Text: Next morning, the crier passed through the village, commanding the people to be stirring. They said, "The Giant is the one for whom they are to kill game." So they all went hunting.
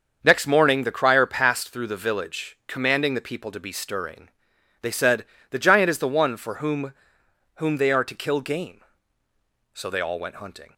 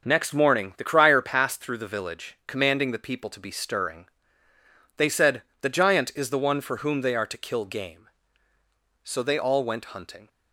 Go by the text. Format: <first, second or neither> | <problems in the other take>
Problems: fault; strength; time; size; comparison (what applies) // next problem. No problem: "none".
second | starts louder than the rest; until 1.2 s; 7 dB; also in the second // says "whom" twice; at 7.5 s